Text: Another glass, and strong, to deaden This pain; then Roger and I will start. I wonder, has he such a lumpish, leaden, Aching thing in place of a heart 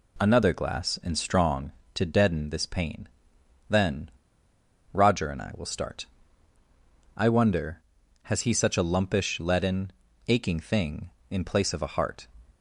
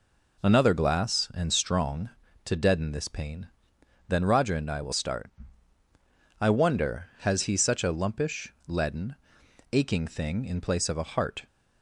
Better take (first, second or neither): second